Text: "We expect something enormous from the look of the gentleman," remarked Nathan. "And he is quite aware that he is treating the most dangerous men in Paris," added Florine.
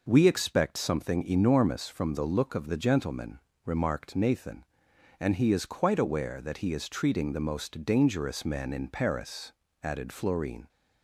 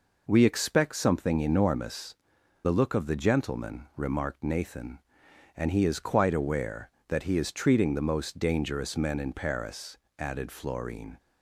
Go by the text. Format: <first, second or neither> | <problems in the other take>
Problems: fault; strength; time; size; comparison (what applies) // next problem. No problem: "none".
first | skips "from"; at 2.4 s